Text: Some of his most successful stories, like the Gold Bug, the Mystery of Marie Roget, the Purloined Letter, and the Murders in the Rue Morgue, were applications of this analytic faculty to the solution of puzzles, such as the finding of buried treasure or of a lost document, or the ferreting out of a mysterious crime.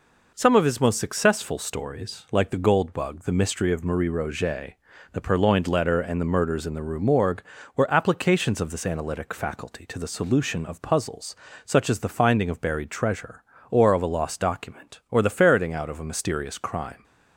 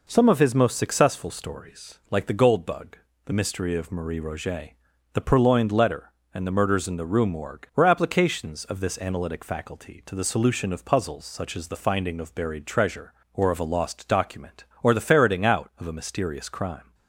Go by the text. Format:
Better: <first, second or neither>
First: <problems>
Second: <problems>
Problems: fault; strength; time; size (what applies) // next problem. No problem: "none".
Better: neither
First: none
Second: none